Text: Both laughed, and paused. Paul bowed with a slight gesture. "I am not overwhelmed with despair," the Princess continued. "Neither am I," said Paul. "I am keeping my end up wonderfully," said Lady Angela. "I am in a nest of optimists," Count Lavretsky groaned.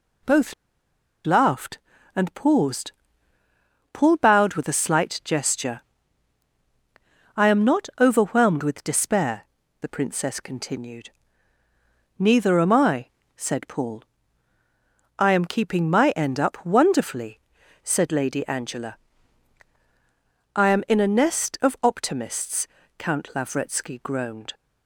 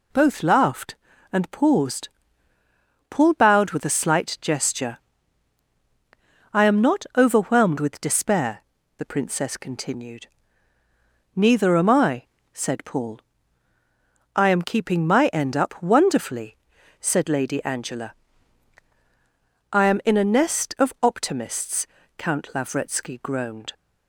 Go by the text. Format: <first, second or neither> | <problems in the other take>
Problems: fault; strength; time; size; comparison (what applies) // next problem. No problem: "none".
second | pauses between "Both" and "laughed"; noticeable; at 0.5 s; 0.71 s long